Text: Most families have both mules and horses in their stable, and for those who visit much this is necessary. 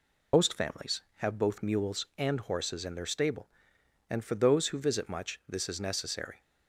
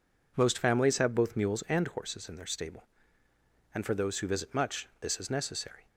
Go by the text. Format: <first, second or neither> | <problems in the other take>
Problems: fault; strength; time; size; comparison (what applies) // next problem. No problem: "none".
second | loses the start of "Most"; at 0.3 s; 95 ms